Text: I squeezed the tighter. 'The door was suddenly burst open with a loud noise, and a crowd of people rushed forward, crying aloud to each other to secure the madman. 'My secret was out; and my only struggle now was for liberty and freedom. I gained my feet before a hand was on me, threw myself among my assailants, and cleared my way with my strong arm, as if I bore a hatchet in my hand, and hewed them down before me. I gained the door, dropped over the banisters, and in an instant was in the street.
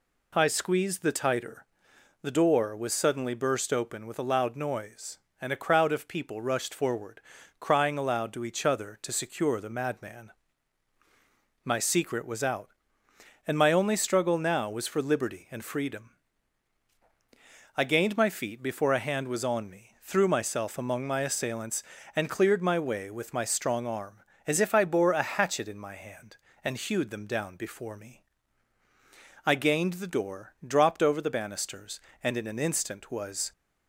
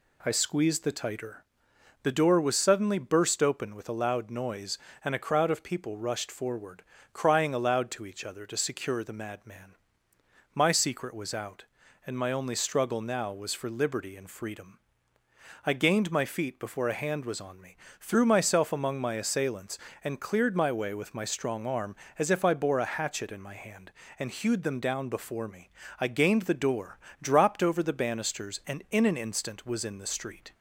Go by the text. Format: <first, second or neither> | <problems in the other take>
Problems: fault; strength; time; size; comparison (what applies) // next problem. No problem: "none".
second | stops before "in the street"; at 33.5 s